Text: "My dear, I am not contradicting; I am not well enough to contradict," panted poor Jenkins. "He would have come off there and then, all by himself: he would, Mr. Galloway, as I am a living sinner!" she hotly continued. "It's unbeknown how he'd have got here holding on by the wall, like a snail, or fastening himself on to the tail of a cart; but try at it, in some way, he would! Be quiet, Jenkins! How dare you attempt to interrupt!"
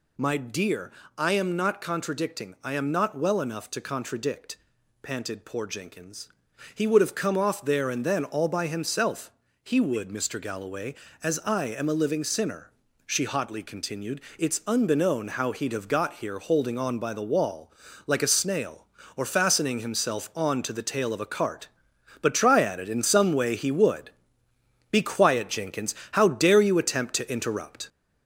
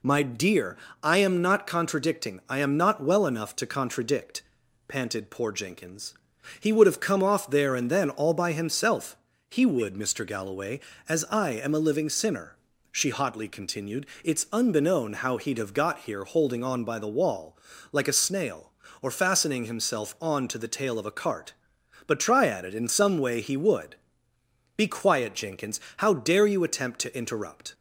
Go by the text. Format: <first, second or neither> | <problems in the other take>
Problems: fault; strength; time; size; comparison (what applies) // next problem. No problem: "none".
second | gets louder; noticeable; throughout; 4.5 dB